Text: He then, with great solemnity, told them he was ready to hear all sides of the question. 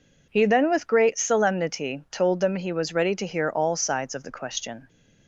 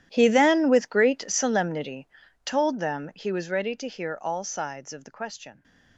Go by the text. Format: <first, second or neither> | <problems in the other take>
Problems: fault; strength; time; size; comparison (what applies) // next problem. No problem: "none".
first | gets quieter; strong; throughout; 18.5 dB